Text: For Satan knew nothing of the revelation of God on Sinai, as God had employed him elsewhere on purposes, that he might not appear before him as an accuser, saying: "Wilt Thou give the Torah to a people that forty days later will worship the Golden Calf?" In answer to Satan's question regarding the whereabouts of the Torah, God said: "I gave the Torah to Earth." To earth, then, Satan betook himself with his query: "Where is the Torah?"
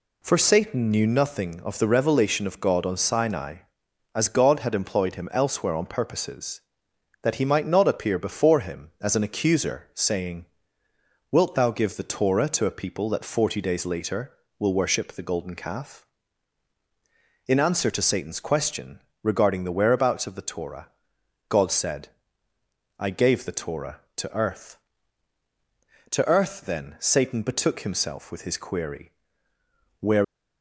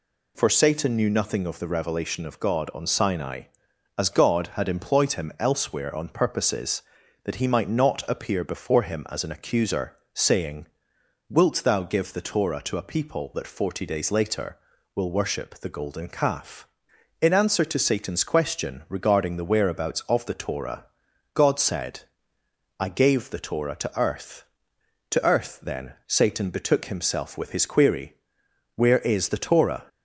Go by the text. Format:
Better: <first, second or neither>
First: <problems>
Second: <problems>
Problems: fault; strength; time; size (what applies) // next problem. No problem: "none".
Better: second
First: pauses between "question" and "regarding"; slight; at 19.0 s; 0.22 s long // stops before "is the Torah"; at 30.2 s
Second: none